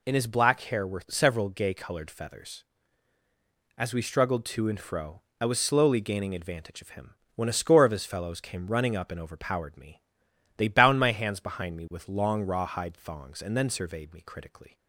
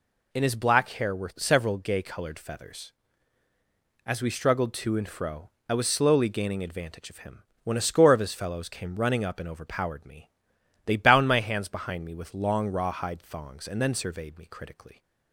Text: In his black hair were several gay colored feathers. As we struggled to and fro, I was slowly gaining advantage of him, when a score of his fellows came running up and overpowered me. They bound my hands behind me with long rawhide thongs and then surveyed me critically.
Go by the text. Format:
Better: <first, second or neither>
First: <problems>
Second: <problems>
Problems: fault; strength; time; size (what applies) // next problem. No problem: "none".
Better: neither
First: none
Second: none